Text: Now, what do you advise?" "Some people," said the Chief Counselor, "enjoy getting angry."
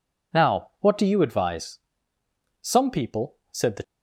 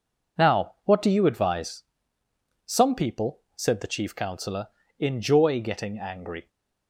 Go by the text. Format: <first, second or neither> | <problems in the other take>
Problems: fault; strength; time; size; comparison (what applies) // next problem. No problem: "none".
second | stops before "Chief Counselor enjoy getting angry"; at 3.8 s